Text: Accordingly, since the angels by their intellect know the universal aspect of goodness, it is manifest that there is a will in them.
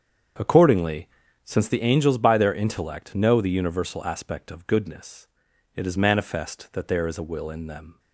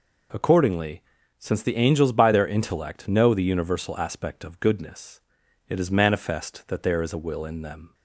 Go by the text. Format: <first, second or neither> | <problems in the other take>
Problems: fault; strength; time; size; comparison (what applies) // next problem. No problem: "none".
second | starts louder than the rest; strong; until 1.8 s; 7.5 dB